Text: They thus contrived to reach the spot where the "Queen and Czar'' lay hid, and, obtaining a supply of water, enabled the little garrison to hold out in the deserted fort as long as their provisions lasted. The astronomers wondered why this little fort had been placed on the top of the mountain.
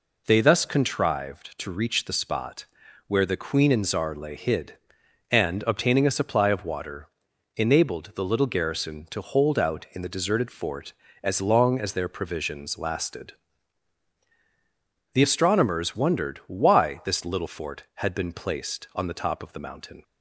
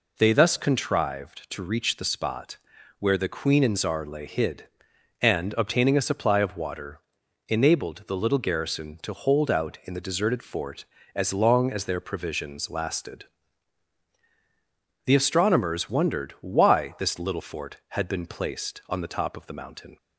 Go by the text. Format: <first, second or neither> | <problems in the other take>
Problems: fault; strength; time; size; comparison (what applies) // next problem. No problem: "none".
neither | pauses between "spot" and "where"; the same in both